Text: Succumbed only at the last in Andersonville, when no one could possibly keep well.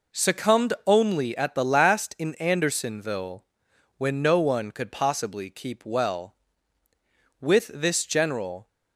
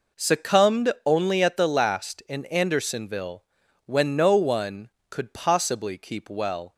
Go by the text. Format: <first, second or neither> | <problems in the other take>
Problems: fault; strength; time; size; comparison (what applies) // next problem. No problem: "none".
second | goes on to say "With this general"; noticeable; from 7.3 s on; 1.2 s long